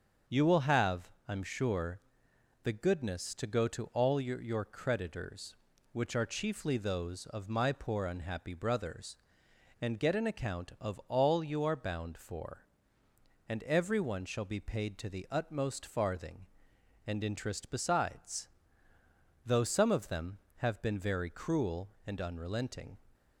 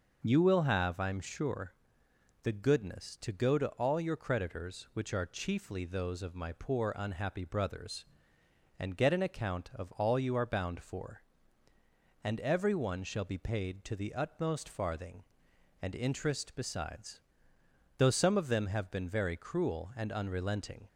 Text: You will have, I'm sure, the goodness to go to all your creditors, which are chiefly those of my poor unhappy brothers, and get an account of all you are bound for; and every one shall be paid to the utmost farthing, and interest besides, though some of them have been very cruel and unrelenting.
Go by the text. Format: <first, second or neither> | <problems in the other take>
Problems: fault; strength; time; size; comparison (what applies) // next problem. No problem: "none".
second | starts louder than the rest; until 1.4 s; 6.5 dB; noticeable in the second // says "your" twice; at 4.4 s